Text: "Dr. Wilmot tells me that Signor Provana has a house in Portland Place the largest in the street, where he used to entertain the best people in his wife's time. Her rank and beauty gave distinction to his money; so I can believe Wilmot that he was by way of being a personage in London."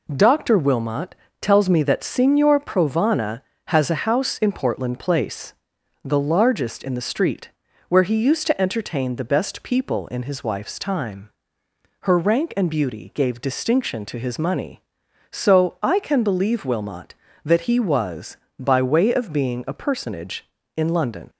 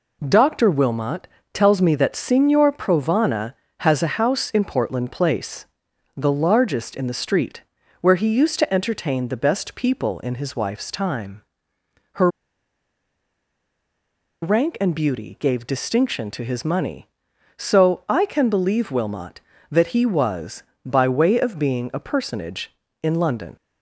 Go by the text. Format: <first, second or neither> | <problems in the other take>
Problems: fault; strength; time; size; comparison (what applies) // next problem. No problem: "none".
first | pauses between "Wilmot" and "tells"; slight; at 1.2 s; 0.24 s long; slight in the first // pauses between "Place" and "the"; noticeable; at 5.6 s; 0.50 s long; noticeable in the first // pauses between "Her" and "rank"; strong; at 12.2 s; 2.1 s long